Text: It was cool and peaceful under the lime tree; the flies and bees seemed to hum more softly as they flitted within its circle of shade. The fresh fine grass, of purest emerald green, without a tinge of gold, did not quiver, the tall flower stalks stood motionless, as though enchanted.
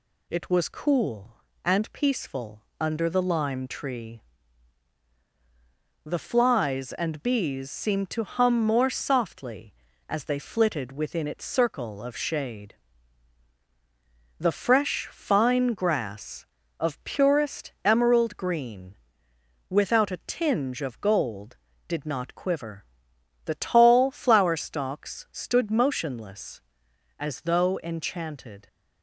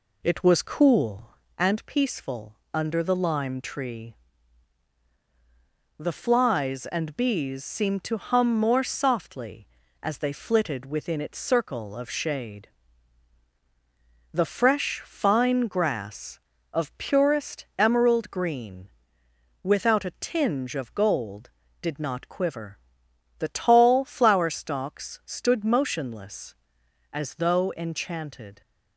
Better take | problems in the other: first | starts louder than the rest; slight; until 1.5 s; 2.5 dB // pauses between "peaceful" and "under"; slight; at 2.5 s; 0.20 s long; slight in the first

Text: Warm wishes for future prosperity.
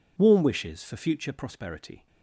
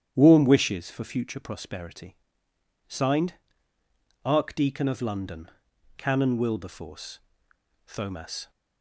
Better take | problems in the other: first | starts louder than the rest; strong; until 1.1 s; 10 dB // goes on to say "Signed ARCHDEACON OF LONDON CANON WILBERFORCE THOMAS"; strong; from 2.8 s on; 5.6 s long

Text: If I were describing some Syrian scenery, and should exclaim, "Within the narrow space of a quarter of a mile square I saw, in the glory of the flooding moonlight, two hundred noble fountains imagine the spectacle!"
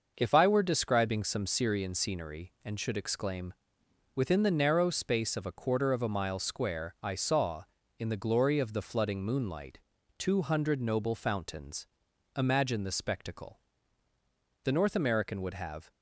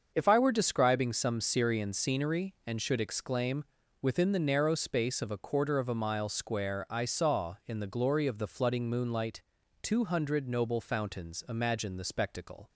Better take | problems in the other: second | starts louder than the rest; noticeable; until 1.1 s; 6 dB; also in the second // pauses between "fountains" and "imagine"; noticeable; at 11.8 s; 0.50 s long // goes on to say "the North American would have"; noticeable; from 14.6 s on; 1.2 s long

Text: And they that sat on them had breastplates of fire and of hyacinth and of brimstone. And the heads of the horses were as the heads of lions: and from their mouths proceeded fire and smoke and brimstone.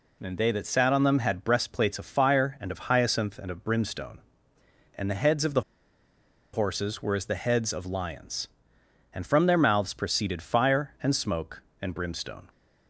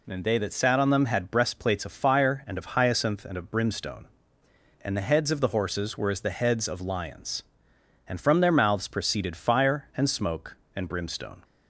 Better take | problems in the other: second | pauses between "the" and "horses"; noticeable; at 5.6 s; 0.92 s long

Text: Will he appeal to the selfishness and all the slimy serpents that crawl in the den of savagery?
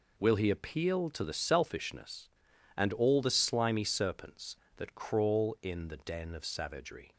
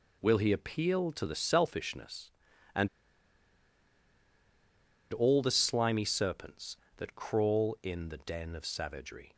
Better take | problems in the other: first | pauses between "and" and "all"; strong; at 2.8 s; 2.2 s long

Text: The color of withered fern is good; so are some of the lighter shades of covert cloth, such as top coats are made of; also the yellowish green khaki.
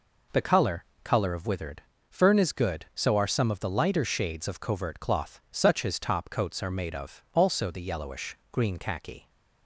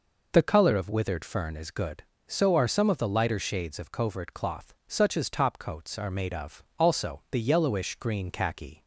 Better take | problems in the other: second | says "color" twice; at 1.0 s // pauses between "withered" and "fern"; slight; at 1.8 s; 0.30 s long

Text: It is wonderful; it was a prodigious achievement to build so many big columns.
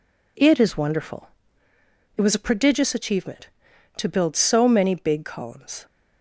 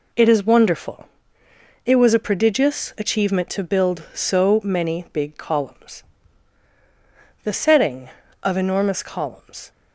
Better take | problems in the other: first | goes on to say "The setting of enormous columns"; strong; from 7.4 s on; 2.2 s long

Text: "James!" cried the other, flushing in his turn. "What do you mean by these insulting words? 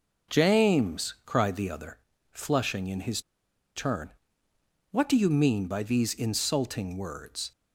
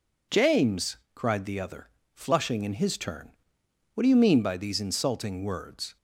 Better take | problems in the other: second | pauses between "his" and "turn"; noticeable; at 3.2 s; 0.53 s long

